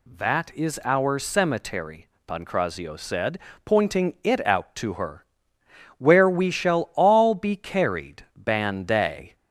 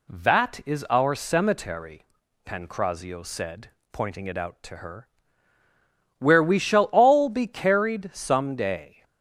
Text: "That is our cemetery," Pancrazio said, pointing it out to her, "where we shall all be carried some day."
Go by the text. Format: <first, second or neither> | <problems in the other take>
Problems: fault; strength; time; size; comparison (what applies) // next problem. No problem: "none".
second | says "ban" for "some"; at 8.3 s